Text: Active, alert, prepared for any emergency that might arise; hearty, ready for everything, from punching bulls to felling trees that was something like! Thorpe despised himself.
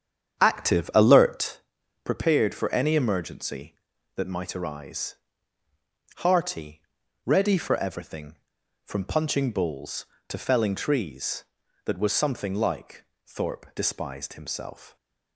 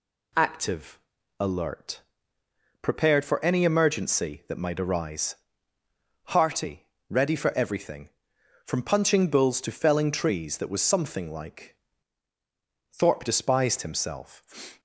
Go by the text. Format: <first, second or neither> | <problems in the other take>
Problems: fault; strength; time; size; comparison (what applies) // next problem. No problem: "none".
second | starts louder than the rest; strong; until 1.6 s; 8.5 dB